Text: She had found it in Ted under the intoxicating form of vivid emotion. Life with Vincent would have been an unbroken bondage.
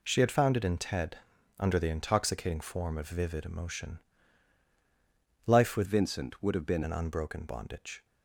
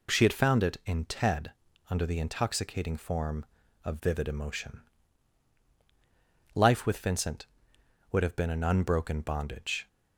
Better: second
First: pauses between "Ted" and "under"; at 1.1 s; 0.40 s long // changes voice from "Vincent" to "been"; from 5.8 to 6.8 s; 1.0 s long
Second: pauses between "Ted" and "under"; slight; at 1.5 s; 0.36 s long

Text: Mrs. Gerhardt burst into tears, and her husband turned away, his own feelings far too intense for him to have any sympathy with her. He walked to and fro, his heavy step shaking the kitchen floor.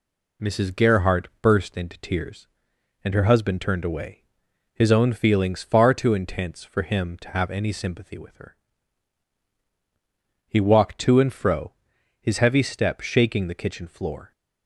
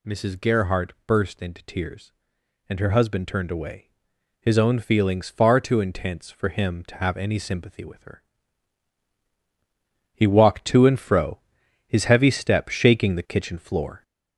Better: first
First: none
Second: gets louder; noticeable; throughout; 4.5 dB

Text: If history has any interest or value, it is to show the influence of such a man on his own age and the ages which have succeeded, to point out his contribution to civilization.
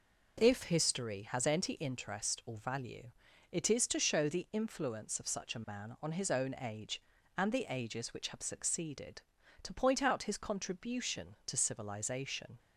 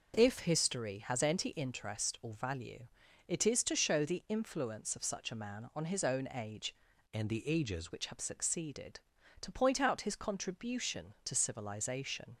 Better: first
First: none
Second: changes voice from "and" to "ages"; from 7.1 to 7.9 s; 0.8 s long

